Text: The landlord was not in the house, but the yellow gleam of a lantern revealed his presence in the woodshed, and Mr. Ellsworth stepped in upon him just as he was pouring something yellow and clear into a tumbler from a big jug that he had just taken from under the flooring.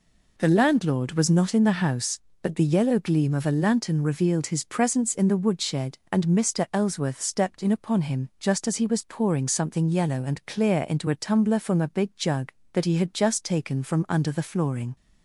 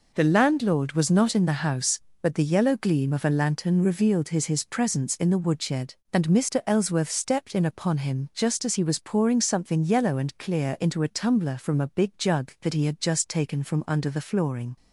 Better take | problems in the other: first | says "his" twice; at 4.4 s

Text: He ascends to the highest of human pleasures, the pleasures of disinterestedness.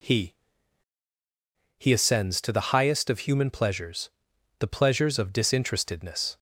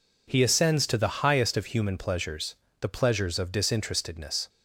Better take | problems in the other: second | says "He" twice; at 1.7 s

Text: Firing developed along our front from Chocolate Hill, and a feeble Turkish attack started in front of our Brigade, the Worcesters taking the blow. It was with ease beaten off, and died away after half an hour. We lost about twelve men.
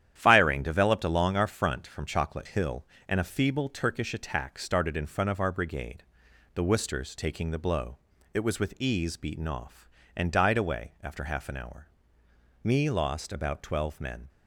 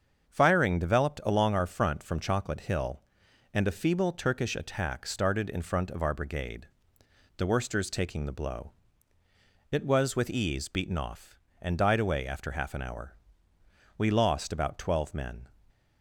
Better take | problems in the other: second | starts louder than the rest; strong; until 1.1 s; 10.5 dB; also in the second // says "Me" for "We"; at 12.6 s

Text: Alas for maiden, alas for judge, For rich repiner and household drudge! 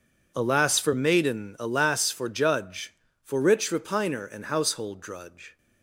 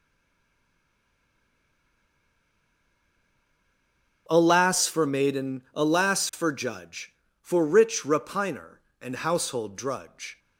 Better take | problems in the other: first | stays silent before the first word; strong; until 4.2 s; 4.2 s long

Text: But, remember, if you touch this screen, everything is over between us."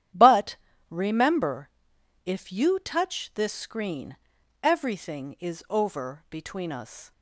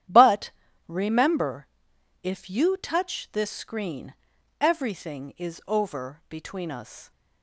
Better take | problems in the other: neither | starts louder than the rest; strong; the same in both

